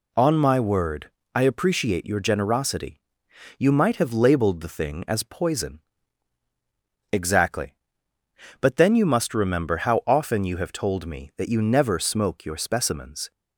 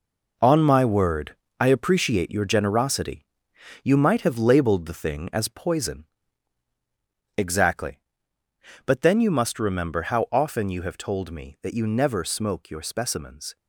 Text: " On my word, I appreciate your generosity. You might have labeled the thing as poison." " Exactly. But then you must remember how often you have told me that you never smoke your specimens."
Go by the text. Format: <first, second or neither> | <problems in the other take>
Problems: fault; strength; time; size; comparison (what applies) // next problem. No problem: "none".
first | gets quieter; strong; throughout; 8.5 dB